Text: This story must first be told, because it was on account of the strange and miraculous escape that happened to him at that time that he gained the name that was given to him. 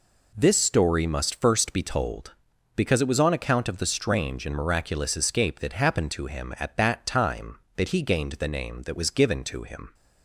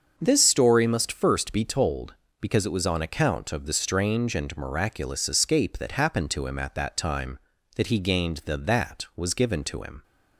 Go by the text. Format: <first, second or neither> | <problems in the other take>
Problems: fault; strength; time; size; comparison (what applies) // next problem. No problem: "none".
first | starts louder than the rest; until 1.1 s; 6.5 dB // skips "name"; at 8.5 s